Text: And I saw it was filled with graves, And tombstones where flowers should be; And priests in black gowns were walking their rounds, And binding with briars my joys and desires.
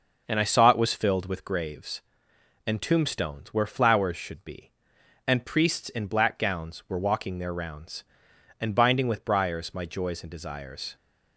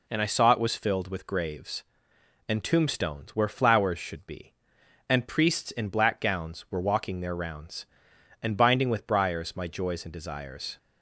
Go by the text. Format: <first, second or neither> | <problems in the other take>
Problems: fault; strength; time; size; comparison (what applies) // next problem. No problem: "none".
second | starts louder than the rest; noticeable; until 1.5 s; 5.5 dB